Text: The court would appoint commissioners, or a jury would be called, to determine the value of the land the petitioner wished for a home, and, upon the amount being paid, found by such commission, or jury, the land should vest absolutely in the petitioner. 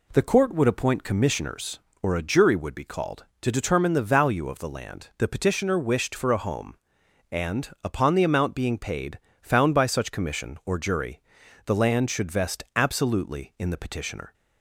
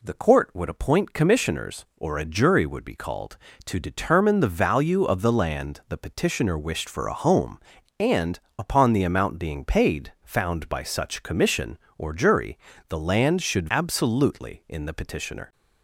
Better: first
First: none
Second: skips "vest"; at 13.7 s

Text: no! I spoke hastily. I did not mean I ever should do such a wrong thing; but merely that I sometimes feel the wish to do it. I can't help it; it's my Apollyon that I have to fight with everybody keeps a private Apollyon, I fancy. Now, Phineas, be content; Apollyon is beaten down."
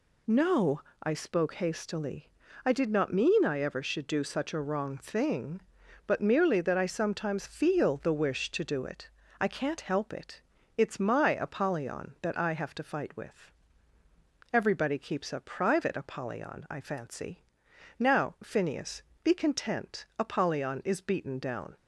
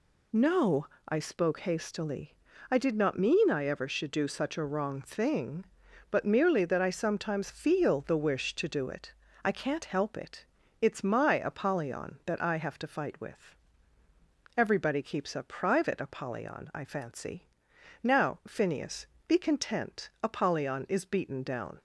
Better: neither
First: pauses between "with" and "everybody"; at 13.5 s; 1.0 s long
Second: pauses between "with" and "everybody"; at 13.5 s; 1.0 s long

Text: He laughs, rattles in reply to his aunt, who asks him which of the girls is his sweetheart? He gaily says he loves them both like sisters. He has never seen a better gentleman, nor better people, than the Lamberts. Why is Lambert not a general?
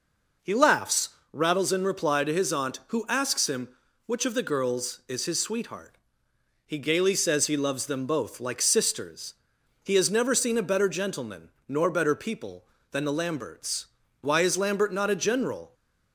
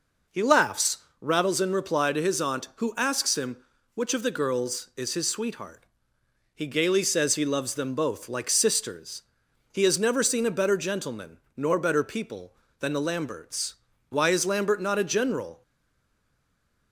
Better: first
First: none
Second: stays silent after the last word; noticeable; from 15.6 s on; 1.3 s long

